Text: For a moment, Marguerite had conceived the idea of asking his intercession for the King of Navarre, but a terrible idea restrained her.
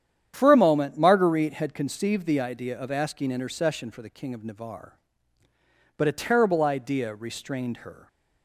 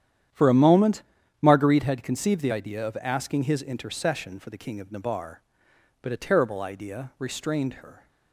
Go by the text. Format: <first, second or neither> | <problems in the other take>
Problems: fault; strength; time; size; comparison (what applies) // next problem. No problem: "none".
second | starts louder than the rest; strong; until 1.3 s; 9.5 dB; strong in the second // skips "his"; at 3.2 s